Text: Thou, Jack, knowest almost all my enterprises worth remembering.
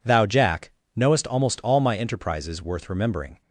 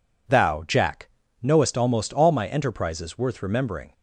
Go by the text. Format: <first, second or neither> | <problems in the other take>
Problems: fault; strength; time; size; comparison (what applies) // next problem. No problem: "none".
neither | none